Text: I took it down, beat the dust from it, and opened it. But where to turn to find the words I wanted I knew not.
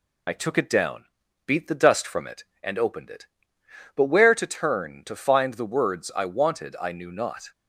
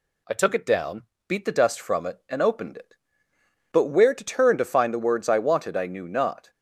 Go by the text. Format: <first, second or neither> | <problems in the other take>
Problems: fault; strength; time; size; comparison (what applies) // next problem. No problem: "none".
second | loses the start of "I"; at 0.2 s; 35 ms